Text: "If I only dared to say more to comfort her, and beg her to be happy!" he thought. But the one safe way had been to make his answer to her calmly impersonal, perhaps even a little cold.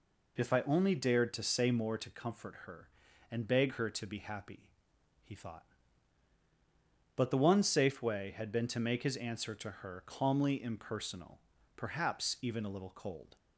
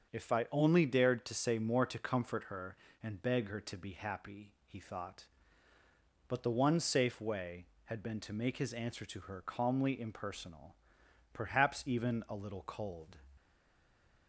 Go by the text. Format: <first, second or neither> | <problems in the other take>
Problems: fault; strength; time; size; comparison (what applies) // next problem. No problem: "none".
first | starts louder than the rest; until 1.1 s; 7 dB // stays silent after the last word; slight; from 13.3 s on; 0.9 s long